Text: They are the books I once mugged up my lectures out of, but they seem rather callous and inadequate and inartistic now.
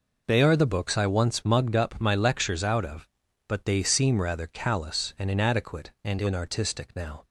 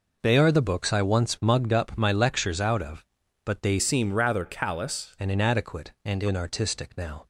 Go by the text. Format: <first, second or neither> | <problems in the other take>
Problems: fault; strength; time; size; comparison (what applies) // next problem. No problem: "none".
first | changes voice from "seem" to "callous"; from 3.7 to 5.1 s; 1.4 s long